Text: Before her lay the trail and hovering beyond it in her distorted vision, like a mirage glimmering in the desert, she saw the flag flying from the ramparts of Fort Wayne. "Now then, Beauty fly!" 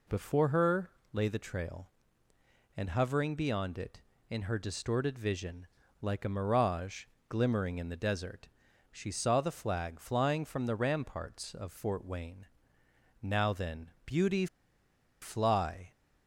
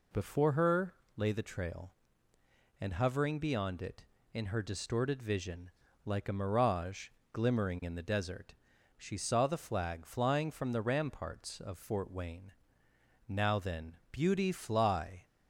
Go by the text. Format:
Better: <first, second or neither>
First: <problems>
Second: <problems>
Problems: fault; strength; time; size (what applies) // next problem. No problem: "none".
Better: second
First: pauses between "her" and "lay"; slight; at 0.9 s; 0.22 s long // pauses between "mirage" and "glimmering"; slight; at 7.0 s; 0.24 s long // pauses between "Beauty" and "fly"; noticeable; at 14.4 s; 0.75 s long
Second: pauses between "her" and "lay"; slight; at 0.9 s; 0.22 s long // pauses between "mirage" and "glimmering"; slight; at 7.0 s; 0.24 s long